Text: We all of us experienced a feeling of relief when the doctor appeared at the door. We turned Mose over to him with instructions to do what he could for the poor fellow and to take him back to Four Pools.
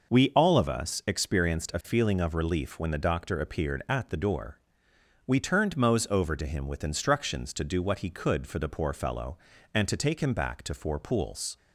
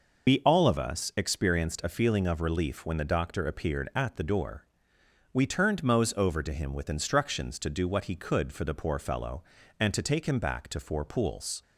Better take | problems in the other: first | loses the start of "We"; at 0.2 s; 65 ms

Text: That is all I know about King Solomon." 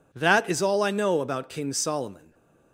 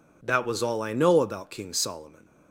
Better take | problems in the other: first | says "was" for "is"; at 0.4 s

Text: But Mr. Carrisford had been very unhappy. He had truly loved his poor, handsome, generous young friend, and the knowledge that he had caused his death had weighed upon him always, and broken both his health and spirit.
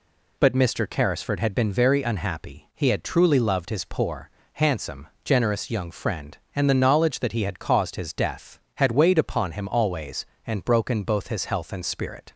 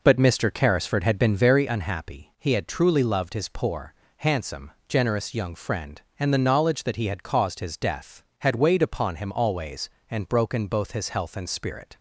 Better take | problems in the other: first | starts louder than the rest; noticeable; until 1.7 s; 4.5 dB

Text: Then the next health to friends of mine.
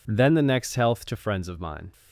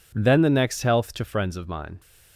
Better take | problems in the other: neither | none

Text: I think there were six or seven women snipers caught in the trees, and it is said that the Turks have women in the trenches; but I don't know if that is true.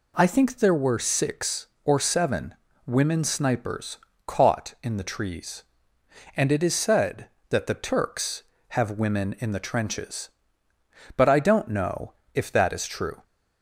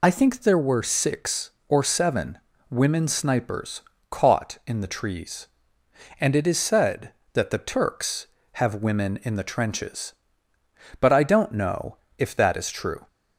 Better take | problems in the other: first | loses the start of "I"; at 0.0 s; 45 ms // pauses between "seven" and "women"; slight; at 2.3 s; 0.32 s long; slight in the first // pauses between "snipers" and "caught"; slight; at 3.8 s; 0.30 s long; slight in the first // pauses between "know" and "if"; slight; at 11.9 s; 0.20 s long; slight in the first

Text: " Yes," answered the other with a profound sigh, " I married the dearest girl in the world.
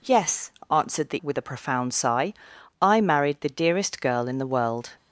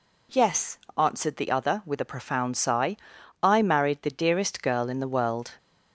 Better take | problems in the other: second | skips "other"; at 1.2 s

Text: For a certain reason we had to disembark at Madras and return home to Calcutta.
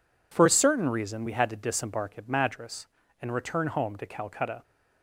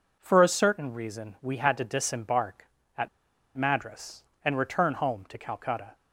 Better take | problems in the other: first | pauses between "at" and "Madras"; noticeable; at 3.0 s; 0.48 s long

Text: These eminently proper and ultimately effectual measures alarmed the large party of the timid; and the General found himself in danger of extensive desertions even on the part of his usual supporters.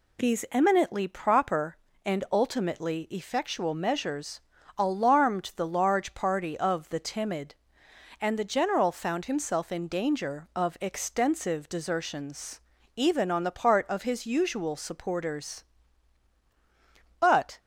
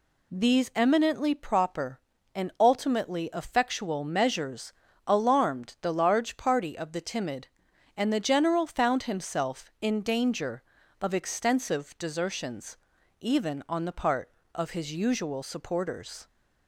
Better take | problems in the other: second | pauses between "measures" and "alarmed"; slight; at 4.4 s; 0.36 s long; slight in the second // pauses between "desertions" and "even"; slight; at 12.5 s; 0.36 s long; also in the second // goes on to say "But"; slight; from 17.1 s on; 0.40 s long

